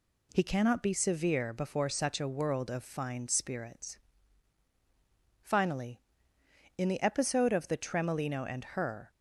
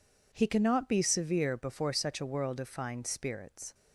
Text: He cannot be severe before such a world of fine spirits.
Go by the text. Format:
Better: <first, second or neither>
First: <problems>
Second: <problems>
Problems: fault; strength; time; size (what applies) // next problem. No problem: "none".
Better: second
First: goes on to say "Finally in the episode of the Tremolino and her"; strong; from 5.4 s on; 3.6 s long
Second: none